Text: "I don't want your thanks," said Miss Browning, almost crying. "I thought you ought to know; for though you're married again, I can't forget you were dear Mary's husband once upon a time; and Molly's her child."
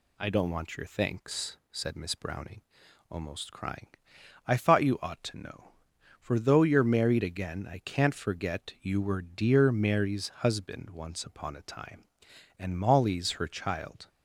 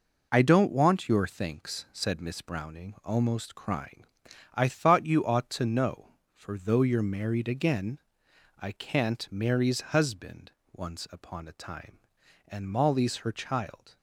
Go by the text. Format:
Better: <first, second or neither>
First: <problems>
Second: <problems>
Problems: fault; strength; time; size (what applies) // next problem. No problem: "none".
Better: first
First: none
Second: skips "forget you were dear"; at 9.3 s // pauses between "husband" and "once"; slight; at 10.5 s; 0.22 s long